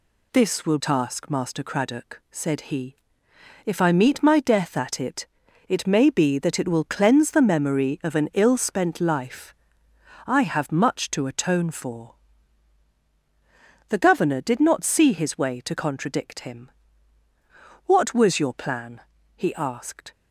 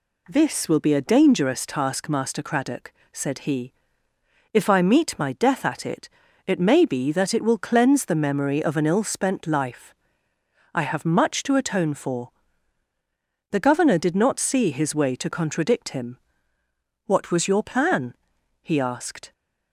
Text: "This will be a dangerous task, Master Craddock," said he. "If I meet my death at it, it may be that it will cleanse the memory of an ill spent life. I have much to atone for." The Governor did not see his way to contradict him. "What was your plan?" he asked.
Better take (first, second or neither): second